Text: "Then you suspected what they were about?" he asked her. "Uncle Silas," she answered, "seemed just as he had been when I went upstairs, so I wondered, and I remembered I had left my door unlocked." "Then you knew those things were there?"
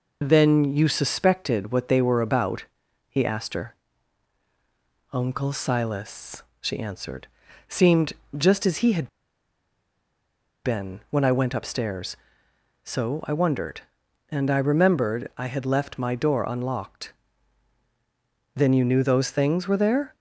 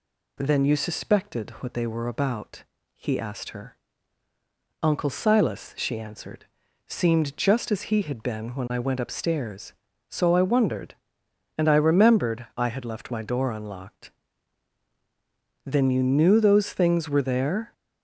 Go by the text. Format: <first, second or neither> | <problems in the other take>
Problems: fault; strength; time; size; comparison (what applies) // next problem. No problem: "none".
second | pauses between "seemed" and "just"; slight; at 8.1 s; 0.26 s long // pauses between "had" and "been"; strong; at 9.0 s; 1.5 s long